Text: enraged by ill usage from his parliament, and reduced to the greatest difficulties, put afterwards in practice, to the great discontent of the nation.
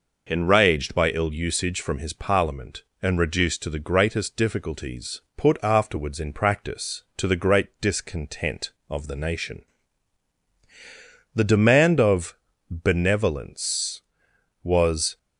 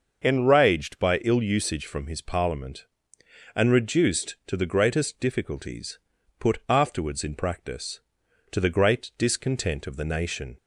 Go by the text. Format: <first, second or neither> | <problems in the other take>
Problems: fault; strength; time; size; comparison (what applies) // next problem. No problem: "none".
second | goes on to say "The demand of benevolence was"; strong; from 11.3 s on; 3.8 s long